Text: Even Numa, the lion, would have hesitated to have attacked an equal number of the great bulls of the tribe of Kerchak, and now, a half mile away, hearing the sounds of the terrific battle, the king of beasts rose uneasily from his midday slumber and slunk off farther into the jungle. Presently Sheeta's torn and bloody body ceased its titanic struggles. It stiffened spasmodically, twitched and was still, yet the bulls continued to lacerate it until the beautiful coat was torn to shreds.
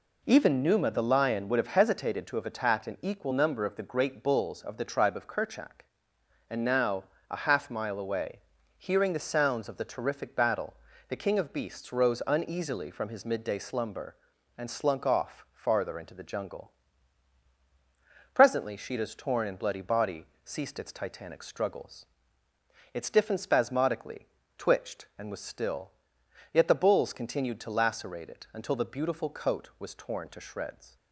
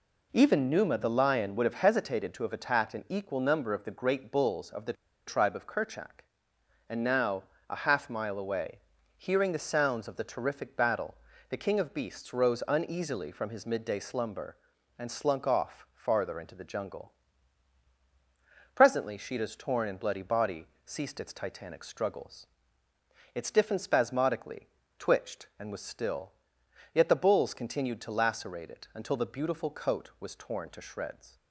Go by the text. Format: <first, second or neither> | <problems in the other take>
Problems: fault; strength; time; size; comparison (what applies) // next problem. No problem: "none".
first | pauses between "the" and "tribe"; slight; at 4.9 s; 0.33 s long // pauses between "body" and "ceased"; slight; at 20.6 s; 0.18 s long; slight in the first